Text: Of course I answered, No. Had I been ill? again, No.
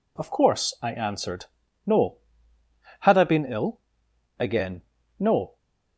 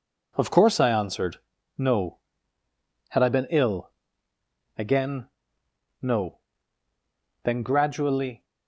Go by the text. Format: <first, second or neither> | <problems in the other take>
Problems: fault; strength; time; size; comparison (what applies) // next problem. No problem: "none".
first | goes on to say "Then gradually"; noticeable; from 7.4 s on; 1.0 s long